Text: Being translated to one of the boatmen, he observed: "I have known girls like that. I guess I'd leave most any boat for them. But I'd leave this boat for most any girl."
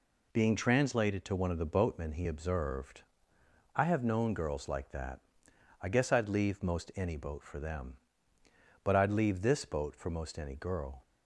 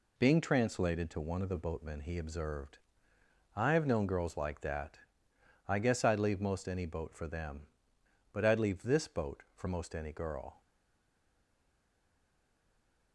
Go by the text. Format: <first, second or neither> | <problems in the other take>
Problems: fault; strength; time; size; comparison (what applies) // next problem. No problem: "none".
first | stays silent after the last word; strong; from 10.6 s on; 2.5 s long